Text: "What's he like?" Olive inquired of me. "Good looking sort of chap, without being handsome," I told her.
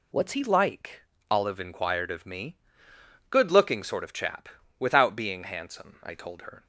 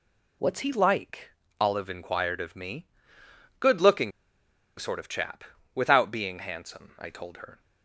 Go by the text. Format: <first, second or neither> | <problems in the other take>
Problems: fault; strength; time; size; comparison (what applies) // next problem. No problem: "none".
first | pauses between "looking" and "sort"; noticeable; at 4.1 s; 0.68 s long